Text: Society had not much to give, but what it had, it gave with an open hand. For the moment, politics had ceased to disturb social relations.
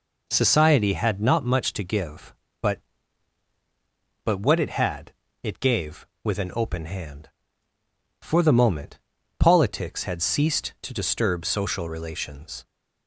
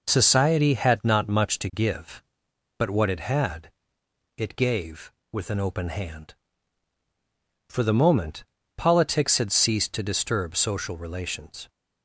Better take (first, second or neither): second